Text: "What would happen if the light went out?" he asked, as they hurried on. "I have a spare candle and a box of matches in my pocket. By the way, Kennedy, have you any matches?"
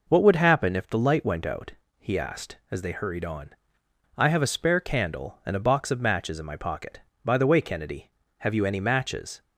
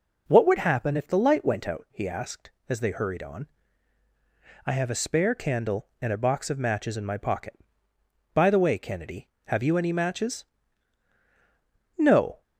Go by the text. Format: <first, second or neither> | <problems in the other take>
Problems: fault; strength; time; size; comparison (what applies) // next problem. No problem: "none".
first | goes on to say "No"; slight; from 11.9 s on; 0.44 s long